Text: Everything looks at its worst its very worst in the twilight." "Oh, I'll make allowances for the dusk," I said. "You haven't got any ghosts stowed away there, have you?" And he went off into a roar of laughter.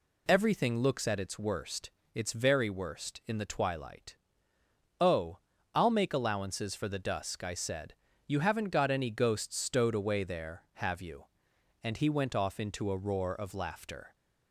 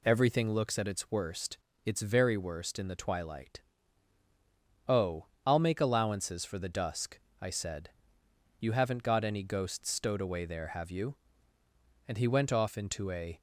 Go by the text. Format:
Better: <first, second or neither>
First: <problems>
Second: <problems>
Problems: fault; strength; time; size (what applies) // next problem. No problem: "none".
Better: first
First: pauses between "worst" and "its"; slight; at 1.9 s; 0.22 s long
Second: pauses between "worst" and "its"; slight; at 1.5 s; 0.28 s long // stops before "roar of laughter"; at 13.3 s